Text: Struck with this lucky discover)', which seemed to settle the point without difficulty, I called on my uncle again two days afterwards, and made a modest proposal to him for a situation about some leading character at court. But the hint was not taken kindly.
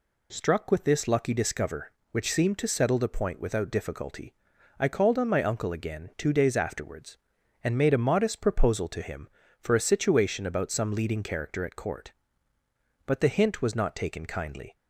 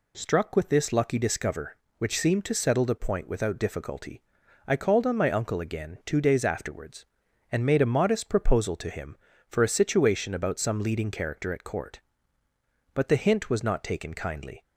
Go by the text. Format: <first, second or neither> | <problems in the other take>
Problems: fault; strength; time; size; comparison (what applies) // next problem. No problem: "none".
neither | none